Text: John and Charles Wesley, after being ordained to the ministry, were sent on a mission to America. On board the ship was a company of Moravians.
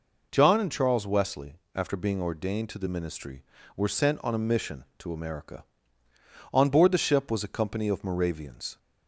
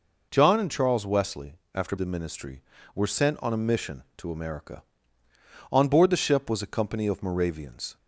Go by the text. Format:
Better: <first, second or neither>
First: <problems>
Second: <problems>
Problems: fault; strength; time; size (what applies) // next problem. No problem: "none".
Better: first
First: none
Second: skips "being ordained to"; at 1.9 s